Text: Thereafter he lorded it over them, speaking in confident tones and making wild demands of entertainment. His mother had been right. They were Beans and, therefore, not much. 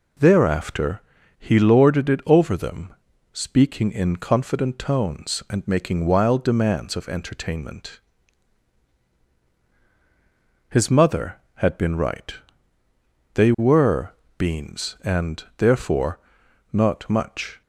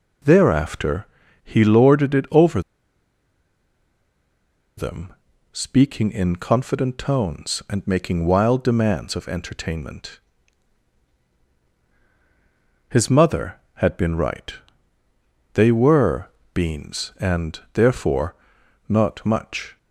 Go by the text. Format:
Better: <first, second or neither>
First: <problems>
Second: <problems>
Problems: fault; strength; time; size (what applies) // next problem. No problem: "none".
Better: first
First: pauses between "Thereafter" and "he"; at 0.9 s; 0.38 s long // pauses between "were" and "Beans"; slight; at 14.1 s; 0.26 s long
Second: pauses between "Thereafter" and "he"; at 1.0 s; 0.38 s long // pauses between "over" and "them"; strong; at 2.6 s; 2.1 s long // pauses between "were" and "Beans"; slight; at 16.2 s; 0.26 s long